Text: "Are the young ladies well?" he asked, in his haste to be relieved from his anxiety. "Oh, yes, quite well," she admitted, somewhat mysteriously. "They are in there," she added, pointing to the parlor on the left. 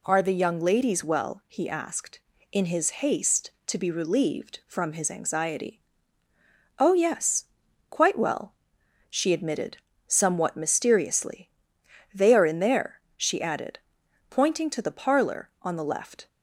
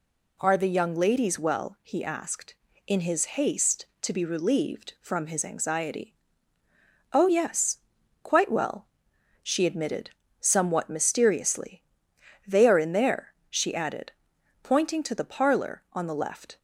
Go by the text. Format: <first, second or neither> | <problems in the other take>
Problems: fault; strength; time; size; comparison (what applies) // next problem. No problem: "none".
neither | none